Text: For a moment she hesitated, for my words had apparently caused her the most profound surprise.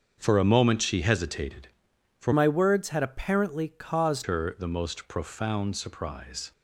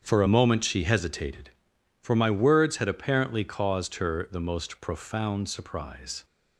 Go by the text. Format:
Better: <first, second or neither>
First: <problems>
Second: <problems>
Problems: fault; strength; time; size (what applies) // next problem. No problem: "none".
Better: second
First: starts louder than the rest; until 1.1 s; 7 dB // changes voice from "my" to "caused"; from 2.3 to 4.2 s; 1.9 s long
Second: starts louder than the rest; strong; until 1.0 s; 7.5 dB